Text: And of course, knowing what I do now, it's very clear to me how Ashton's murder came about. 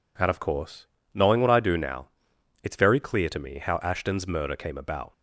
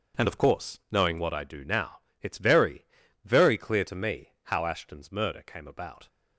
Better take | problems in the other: first | says "very" twice; at 3.2 s

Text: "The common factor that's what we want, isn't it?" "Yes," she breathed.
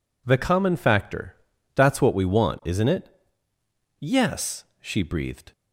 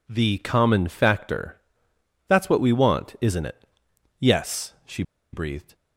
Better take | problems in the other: first | pauses between "factor" and "that's"; noticeable; at 1.6 s; 0.66 s long; also in the first // pauses between "she" and "breathed"; slight; at 5.0 s; 0.30 s long

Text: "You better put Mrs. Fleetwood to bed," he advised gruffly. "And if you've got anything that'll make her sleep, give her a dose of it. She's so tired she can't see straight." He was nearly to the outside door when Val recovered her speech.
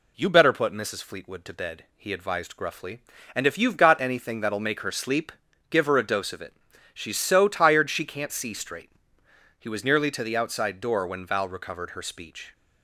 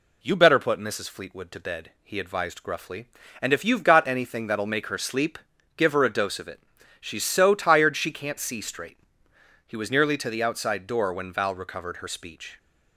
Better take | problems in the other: neither | none

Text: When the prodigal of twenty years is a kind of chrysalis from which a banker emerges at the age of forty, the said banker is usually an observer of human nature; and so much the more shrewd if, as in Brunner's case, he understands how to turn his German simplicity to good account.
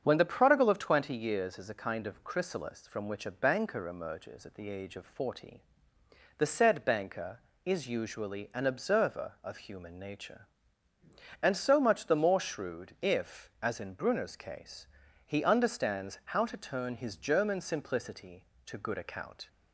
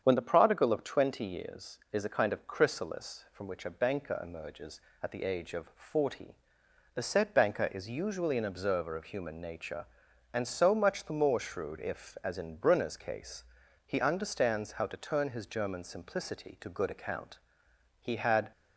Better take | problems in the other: first | starts louder than the rest; strong; until 1.0 s; 8 dB; strong in the first // goes on to say "He had"; from 18.0 s on; 0.50 s long

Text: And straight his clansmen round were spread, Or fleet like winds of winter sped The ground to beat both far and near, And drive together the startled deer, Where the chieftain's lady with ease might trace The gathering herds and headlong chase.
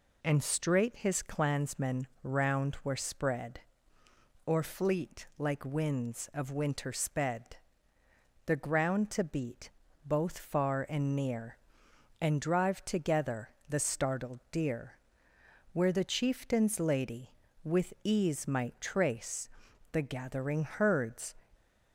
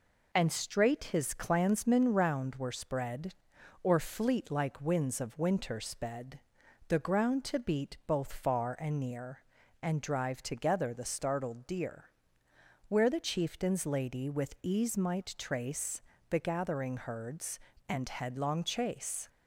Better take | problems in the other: second | pauses between "clansmen" and "round"; slight; at 2.0 s; 0.16 s long // pauses between "sped" and "The"; noticeable; at 7.5 s; 0.88 s long; noticeable in the second // pauses between "beat" and "both"; slight; at 9.7 s; 0.34 s long // pauses between "together" and "the"; slight; at 13.4 s; 0.20 s long // pauses between "trace" and "The"; at 19.4 s; 0.44 s long; slight in the second // stops before "and headlong chase"; at 21.5 s

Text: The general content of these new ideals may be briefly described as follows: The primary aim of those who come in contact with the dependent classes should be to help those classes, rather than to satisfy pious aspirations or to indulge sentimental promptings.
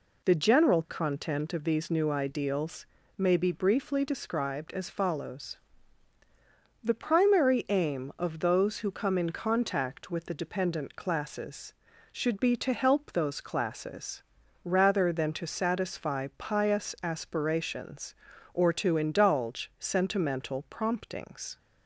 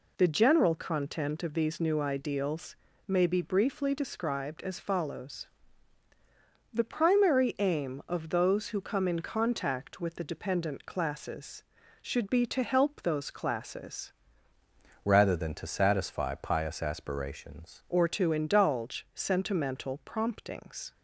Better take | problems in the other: first | pauses between "ideals" and "may"; slight; at 2.7 s; 0.28 s long; slight in the first // changes voice from "rather" to "aspirations"; from 15.0 to 17.8 s; 2.8 s long

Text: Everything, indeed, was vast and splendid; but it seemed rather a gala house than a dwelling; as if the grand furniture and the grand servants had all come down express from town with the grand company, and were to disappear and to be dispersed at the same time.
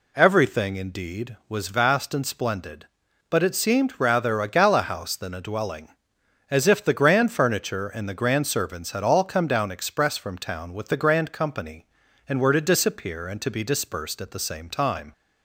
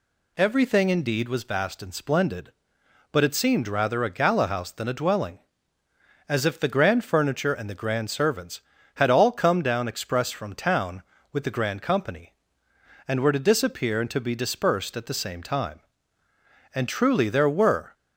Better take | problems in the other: first | goes on to say "And truly there were"; noticeable; from 16.7 s on; 1.2 s long

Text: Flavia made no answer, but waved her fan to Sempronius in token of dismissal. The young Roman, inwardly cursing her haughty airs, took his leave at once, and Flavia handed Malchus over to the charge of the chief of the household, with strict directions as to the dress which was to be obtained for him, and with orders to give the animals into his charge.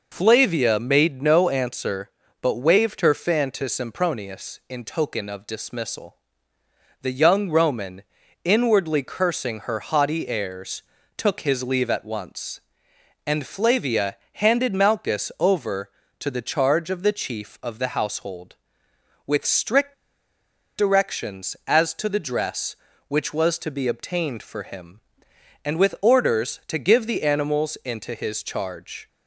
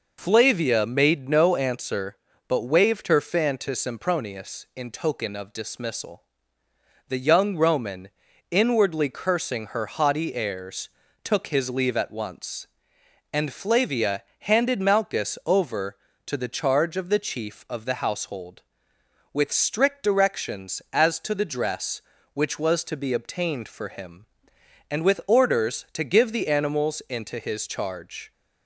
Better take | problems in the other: second | pauses between "Flavia" and "handed"; slight; at 14.1 s; 0.16 s long; slight in the second // pauses between "strict" and "directions"; noticeable; at 19.9 s; 0.82 s long

